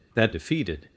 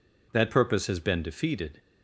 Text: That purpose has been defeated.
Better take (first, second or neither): second